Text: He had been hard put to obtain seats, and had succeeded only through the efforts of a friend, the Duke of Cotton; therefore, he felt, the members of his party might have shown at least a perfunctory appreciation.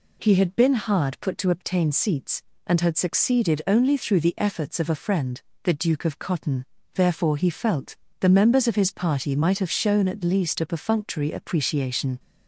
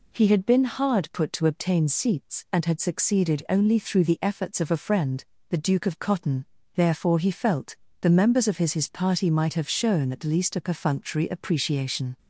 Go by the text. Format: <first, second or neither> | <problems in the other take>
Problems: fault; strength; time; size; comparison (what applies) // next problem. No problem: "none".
first | says "his" twice; at 8.7 s